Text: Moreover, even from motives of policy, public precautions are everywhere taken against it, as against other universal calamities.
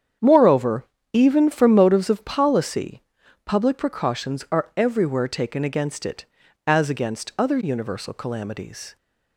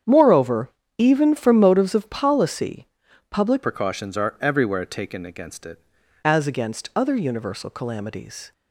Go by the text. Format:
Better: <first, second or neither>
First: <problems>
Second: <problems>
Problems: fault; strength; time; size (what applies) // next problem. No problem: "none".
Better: first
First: starts louder than the rest; strong; until 1.4 s; 8.5 dB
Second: starts louder than the rest; strong; until 1.3 s; 8.5 dB // changes voice from "precautions" to "it"; from 3.6 to 5.7 s; 2.1 s long